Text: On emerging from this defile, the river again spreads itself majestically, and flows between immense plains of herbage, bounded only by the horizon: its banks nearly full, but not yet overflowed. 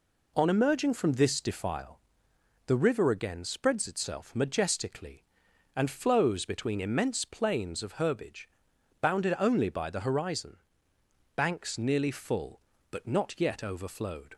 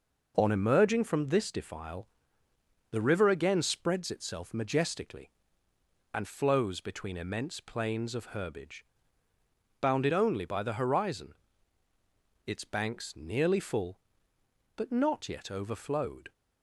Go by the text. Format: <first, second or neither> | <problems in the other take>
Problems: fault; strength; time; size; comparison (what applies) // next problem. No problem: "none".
second | skips "its"; at 10.9 s